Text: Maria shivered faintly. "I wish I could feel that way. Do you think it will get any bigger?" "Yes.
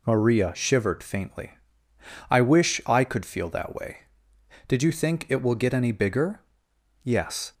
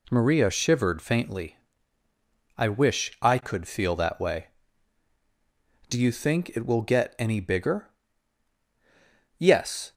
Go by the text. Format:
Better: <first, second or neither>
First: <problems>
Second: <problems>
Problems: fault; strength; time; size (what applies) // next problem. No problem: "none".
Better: second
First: says "Did" for "Do"; at 4.6 s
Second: none